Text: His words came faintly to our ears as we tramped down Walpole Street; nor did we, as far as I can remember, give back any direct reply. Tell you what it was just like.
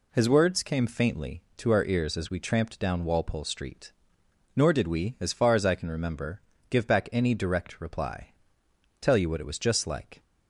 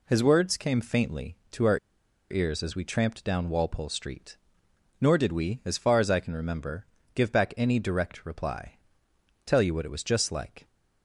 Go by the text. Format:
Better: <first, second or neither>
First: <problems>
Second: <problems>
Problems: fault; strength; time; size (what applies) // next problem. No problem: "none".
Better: first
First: none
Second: pauses between "our" and "ears"; noticeable; at 1.7 s; 0.52 s long